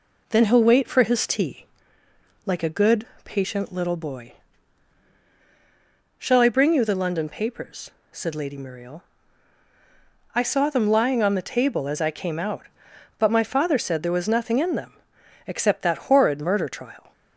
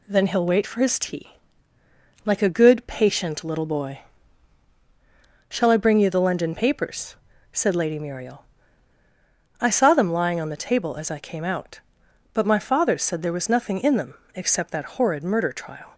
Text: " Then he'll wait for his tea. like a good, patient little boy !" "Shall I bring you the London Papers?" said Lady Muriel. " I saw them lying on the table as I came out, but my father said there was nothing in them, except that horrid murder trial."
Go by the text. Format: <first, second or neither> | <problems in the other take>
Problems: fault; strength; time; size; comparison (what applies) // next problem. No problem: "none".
neither | none